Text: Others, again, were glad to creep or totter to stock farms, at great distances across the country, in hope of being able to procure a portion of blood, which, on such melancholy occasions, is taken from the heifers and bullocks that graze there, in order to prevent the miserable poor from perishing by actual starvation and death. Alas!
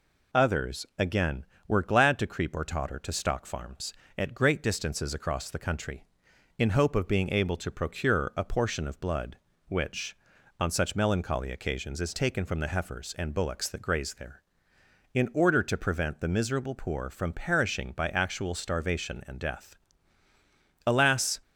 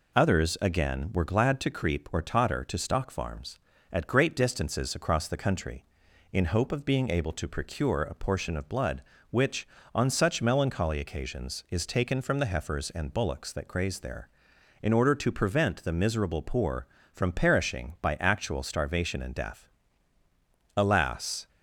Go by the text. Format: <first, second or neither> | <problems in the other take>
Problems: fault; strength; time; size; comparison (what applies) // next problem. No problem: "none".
neither | none